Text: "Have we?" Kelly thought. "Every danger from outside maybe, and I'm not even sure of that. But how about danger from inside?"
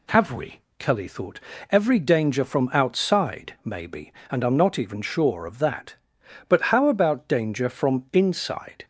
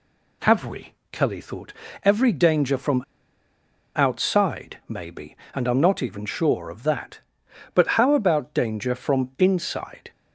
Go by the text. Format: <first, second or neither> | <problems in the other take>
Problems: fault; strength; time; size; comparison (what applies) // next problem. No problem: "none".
first | pauses between "from" and "outside"; noticeable; at 3.0 s; 0.92 s long